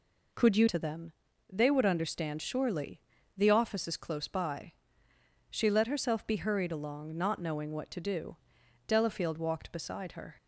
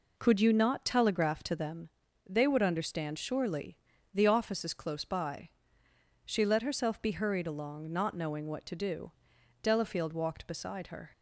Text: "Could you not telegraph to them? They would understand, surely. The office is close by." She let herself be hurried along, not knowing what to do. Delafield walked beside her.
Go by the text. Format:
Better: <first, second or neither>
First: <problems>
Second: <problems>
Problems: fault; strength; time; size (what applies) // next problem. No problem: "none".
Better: second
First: skips "not telegraph"; at 0.6 s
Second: none